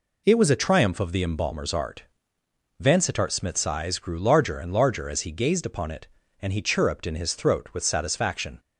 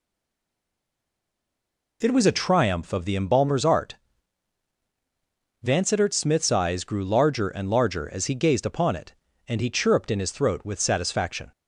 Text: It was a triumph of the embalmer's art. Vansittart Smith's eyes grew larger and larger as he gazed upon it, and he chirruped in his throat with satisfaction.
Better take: first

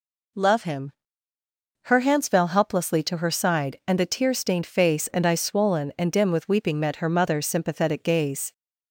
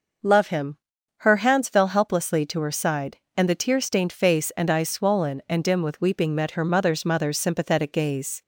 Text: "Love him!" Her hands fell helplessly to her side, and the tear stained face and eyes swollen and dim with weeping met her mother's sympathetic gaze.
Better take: first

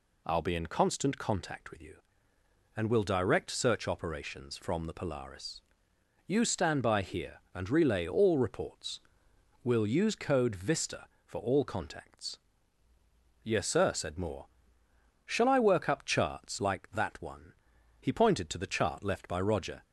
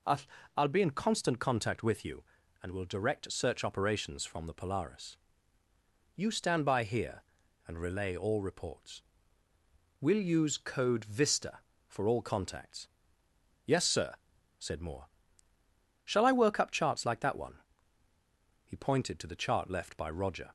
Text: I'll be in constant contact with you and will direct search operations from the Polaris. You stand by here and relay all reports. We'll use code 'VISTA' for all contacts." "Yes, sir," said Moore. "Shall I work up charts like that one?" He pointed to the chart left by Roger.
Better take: first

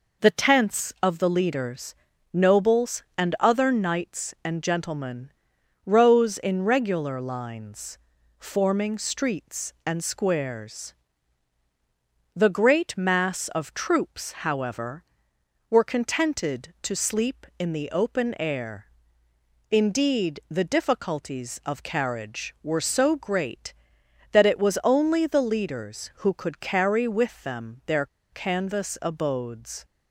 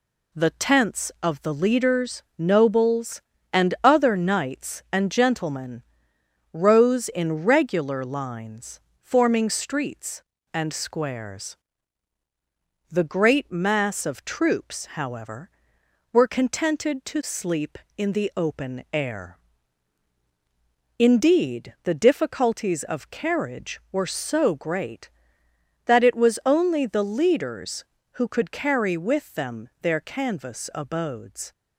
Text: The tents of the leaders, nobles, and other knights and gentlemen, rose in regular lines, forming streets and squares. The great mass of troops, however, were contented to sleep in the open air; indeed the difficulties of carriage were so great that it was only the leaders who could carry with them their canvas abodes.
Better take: second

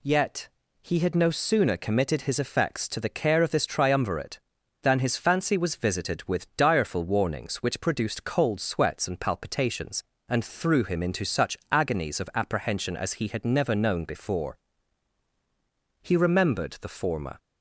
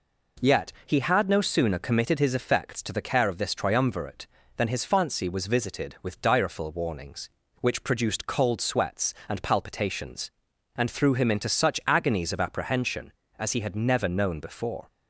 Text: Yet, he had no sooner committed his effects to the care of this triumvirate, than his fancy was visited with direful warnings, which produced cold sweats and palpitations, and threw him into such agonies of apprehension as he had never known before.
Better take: second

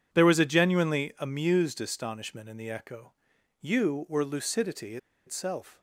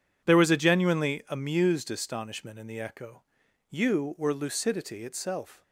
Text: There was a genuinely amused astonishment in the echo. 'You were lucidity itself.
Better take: second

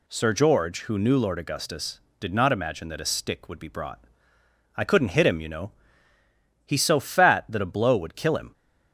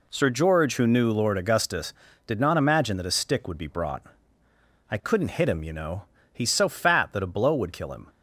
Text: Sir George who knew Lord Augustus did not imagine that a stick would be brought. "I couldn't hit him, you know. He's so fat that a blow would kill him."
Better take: neither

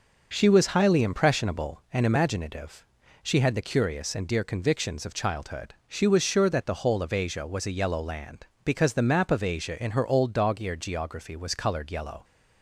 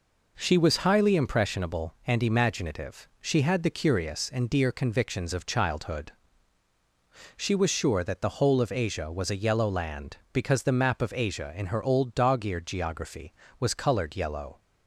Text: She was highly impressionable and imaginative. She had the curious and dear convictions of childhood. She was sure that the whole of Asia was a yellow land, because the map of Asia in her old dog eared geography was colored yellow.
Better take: neither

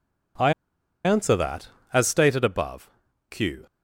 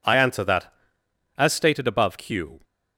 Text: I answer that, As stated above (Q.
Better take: second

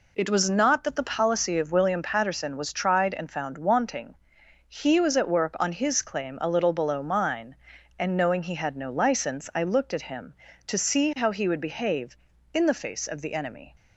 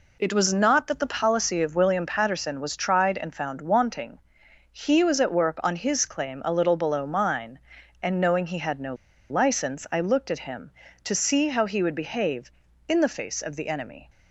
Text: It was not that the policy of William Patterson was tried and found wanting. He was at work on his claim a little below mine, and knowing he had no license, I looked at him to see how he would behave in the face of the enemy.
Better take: first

